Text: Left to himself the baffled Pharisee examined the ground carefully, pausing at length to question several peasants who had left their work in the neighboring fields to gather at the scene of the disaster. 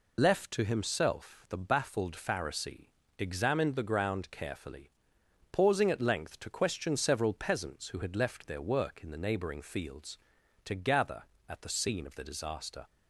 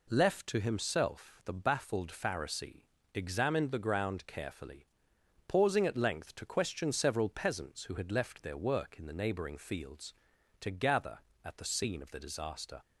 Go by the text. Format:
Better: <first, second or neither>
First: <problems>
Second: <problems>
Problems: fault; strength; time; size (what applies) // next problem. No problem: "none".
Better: second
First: loses the start of "Left"; at 0.1 s; 65 ms // pauses between "Pharisee" and "examined"; slight; at 2.8 s; 0.28 s long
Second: pauses between "Pharisee" and "examined"; slight; at 2.8 s; 0.28 s long